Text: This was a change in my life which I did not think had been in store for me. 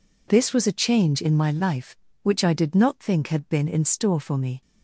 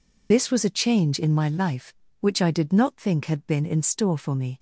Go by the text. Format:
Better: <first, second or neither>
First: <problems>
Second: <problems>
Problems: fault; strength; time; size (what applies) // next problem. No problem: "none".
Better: first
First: none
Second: loses the start of "This"; at 0.3 s; 45 ms